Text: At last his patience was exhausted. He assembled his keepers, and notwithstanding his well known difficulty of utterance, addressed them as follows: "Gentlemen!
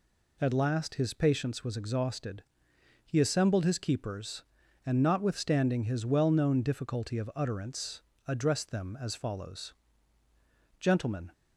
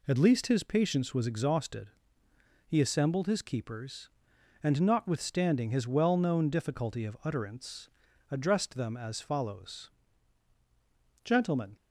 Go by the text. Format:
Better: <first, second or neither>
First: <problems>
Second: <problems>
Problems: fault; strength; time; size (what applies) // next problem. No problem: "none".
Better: first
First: none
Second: says "least" for "last"; at 0.1 s